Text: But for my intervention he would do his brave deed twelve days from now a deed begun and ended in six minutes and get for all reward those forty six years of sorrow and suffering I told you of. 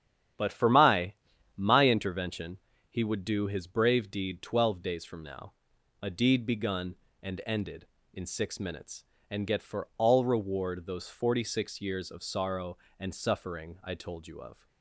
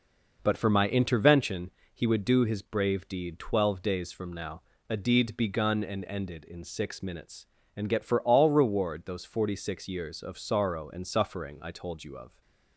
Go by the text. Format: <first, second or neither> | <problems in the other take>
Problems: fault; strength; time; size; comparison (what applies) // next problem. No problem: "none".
second | starts louder than the rest; strong; until 1.7 s; 9.5 dB // says "my" twice; at 1.5 s // pauses between "intervention" and "he"; slight; at 2.5 s; 0.32 s long; slight in the second // pauses between "now" and "a"; noticeable; at 5.5 s; 0.48 s long; slight in the second